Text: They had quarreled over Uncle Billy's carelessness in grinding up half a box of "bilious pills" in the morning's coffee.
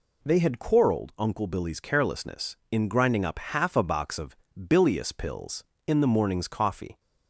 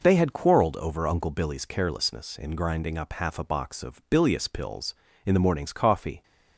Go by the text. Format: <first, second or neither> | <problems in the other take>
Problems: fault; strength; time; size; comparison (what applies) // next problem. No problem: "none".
second | skips "over"; at 1.1 s // pauses between "of" and "bilious"; slight; at 4.3 s; 0.20 s long